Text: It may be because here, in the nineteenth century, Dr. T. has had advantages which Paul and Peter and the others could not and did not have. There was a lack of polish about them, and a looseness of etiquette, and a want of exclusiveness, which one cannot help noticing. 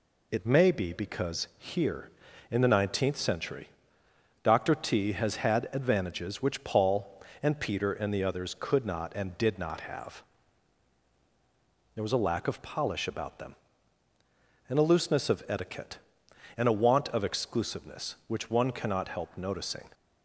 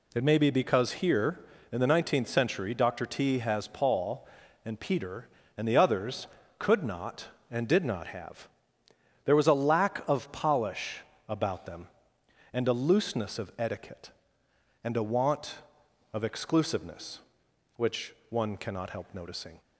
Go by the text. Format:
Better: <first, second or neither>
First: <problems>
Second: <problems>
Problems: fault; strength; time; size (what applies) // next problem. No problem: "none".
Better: first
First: none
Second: skips "had advantages which"; at 3.6 s // pauses between "polish" and "about"; slight; at 11.0 s; 0.26 s long // pauses between "which" and "one"; slight; at 18.1 s; 0.18 s long